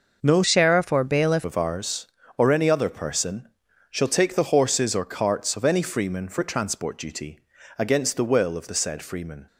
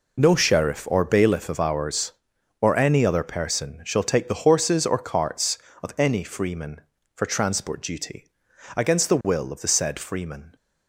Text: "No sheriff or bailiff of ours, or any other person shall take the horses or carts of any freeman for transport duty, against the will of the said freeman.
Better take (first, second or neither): second